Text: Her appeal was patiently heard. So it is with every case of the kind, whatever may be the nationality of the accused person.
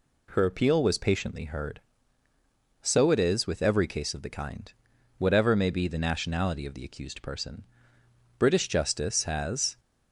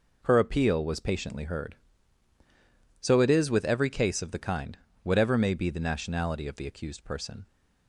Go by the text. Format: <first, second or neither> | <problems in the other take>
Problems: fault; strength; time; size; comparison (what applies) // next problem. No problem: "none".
second | goes on to say "British justice has"; from 8.3 s on; 1.4 s long